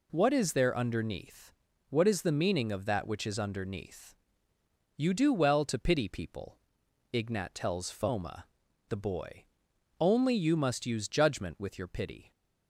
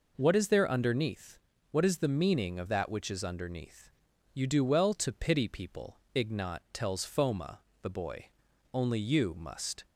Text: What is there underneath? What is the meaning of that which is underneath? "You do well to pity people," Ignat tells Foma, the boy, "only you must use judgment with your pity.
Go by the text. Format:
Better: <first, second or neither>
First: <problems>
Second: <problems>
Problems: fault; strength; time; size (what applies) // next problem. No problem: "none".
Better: first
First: none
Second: stops before "use judgment with your pity"; at 9.8 s